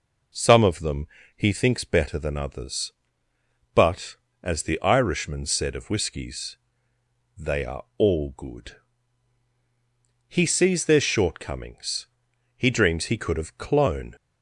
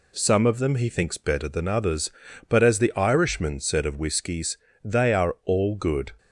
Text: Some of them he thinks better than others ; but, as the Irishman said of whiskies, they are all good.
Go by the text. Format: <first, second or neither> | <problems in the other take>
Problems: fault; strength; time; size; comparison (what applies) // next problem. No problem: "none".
second | pauses between "them" and "he"; slight; at 1.0 s; 0.30 s long // goes on to say "He sees their shortcomings He dreams he could have clone"; strong; from 10.2 s on; 3.8 s long